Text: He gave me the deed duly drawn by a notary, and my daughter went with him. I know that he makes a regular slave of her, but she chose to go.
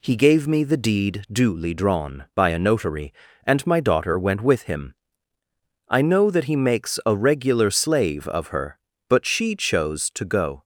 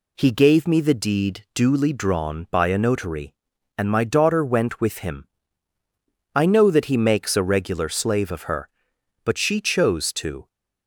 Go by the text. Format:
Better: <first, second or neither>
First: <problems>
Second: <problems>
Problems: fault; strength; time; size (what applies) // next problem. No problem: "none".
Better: first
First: none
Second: stops before "go"; at 10.4 s